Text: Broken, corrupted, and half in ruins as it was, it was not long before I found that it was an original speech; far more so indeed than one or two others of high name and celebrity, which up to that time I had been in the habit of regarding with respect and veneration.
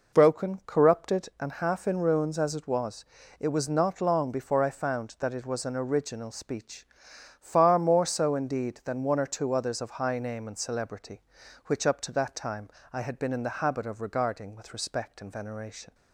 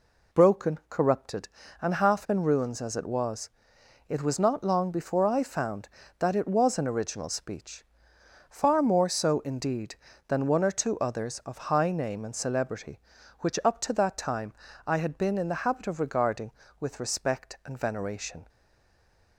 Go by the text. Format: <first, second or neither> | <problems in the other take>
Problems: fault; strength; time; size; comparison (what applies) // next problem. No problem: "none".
first | pauses between "time" and "I"; slight; at 14.5 s; 0.36 s long; slight in the first // stays silent after the last word; slight; from 18.4 s on; 0.9 s long